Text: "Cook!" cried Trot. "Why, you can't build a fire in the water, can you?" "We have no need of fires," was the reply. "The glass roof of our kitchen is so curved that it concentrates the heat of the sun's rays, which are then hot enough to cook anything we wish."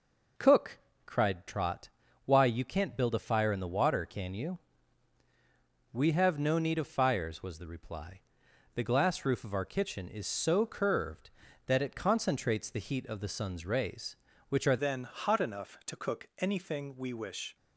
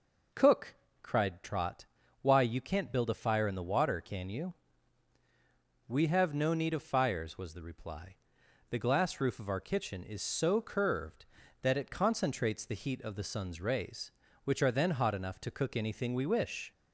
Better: second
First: changes voice at "then"; from 14.7 s on; 2.8 s long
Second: none

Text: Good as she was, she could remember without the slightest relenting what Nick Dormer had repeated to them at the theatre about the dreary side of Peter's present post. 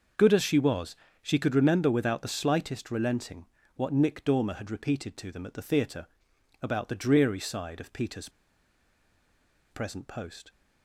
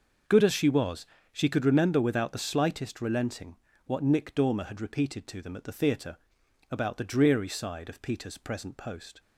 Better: second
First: starts louder than the rest; until 1.4 s; 6 dB // pauses between "relenting" and "what"; slight; at 3.4 s; 0.28 s long // pauses between "theatre" and "about"; noticeable; at 6.0 s; 0.56 s long // pauses between "Peter's" and "present"; strong; at 8.2 s; 1.4 s long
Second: starts louder than the rest; noticeable; until 1.5 s; 6 dB // pauses between "relenting" and "what"; slight; at 3.5 s; 0.28 s long // pauses between "theatre" and "about"; noticeable; at 6.1 s; 0.54 s long

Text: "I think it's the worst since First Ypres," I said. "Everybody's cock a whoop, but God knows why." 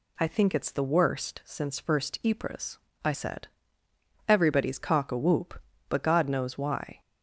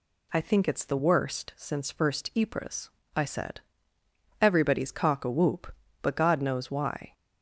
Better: neither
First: none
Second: none

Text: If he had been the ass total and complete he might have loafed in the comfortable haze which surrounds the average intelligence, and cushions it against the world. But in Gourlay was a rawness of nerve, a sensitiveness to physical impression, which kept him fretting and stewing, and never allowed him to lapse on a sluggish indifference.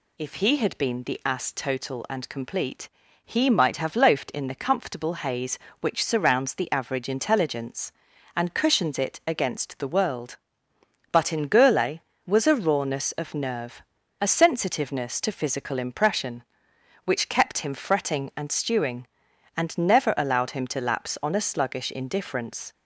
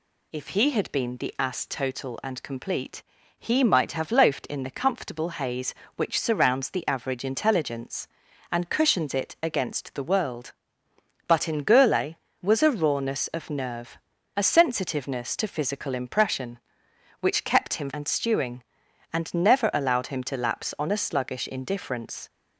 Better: first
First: pauses between "complete" and "he"; slight; at 2.8 s; 0.36 s long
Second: pauses between "complete" and "he"; slight; at 3.0 s; 0.36 s long // skips "fretting"; at 17.9 s

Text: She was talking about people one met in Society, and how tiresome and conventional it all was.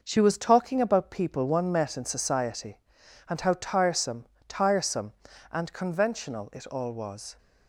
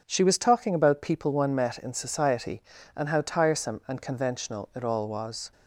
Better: second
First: says "tiresome" twice; at 4.4 s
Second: none

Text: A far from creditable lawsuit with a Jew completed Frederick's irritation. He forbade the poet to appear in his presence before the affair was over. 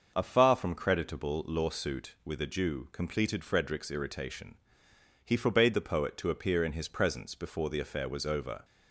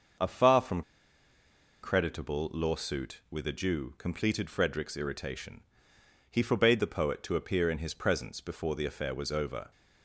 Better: first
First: starts louder than the rest; until 1.1 s; 6.5 dB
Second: starts louder than the rest; until 2.2 s; 6.5 dB // pauses between "from" and "creditable"; at 0.8 s; 1.0 s long

